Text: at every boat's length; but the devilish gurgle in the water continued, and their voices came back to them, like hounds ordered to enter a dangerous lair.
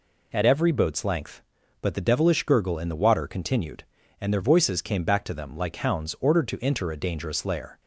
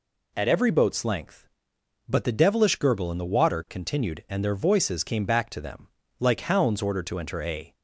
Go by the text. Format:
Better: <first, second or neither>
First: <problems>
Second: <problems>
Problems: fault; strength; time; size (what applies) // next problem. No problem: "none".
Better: first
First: none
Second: stops before "dangerous lair"; at 7.7 s